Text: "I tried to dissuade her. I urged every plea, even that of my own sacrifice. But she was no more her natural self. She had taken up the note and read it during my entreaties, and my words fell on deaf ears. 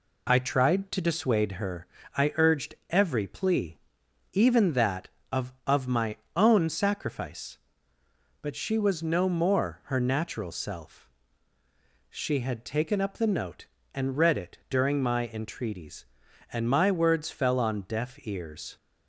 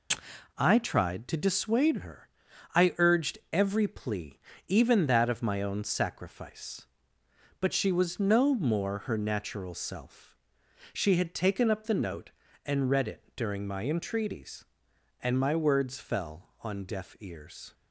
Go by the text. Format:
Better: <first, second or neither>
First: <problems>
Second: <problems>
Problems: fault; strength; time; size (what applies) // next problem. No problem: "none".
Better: second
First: pauses between "urged" and "every"; slight; at 2.7 s; 0.16 s long // says "of" twice; at 5.6 s // pauses between "my" and "own"; slight; at 6.1 s; 0.18 s long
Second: none